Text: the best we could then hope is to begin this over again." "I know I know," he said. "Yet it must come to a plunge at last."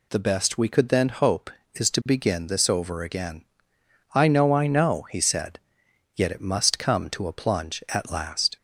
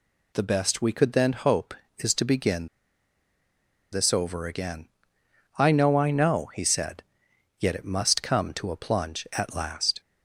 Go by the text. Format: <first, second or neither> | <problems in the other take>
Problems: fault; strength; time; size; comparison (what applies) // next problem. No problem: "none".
first | pauses between "begin" and "this"; at 2.6 s; 1.2 s long